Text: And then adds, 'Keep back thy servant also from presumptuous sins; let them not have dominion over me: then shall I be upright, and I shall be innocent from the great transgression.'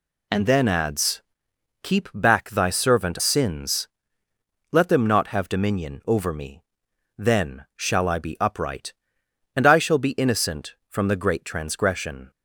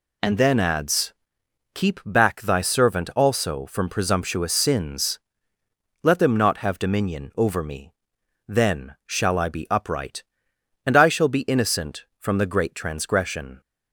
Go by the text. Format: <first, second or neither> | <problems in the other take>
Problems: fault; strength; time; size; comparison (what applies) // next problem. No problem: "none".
second | skips "also from presumptuous"; at 3.2 s